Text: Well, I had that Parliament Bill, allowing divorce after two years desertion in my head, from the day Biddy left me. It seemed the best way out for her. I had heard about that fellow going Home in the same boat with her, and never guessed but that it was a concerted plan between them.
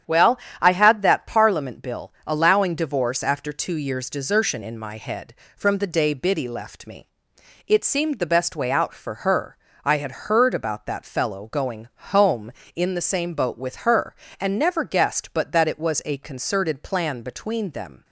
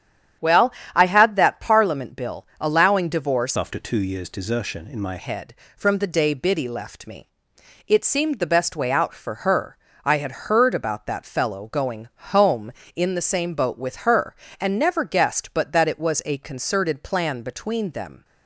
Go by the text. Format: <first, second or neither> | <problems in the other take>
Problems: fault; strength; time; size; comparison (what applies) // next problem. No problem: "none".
first | starts louder than the rest; strong; until 1.6 s; 9 dB; strong in the first // changes voice from "after" to "my"; from 3.5 to 5.1 s; 1.6 s long // pauses between "going" and "Home"; slight; at 12.0 s; 0.24 s long; slight in the first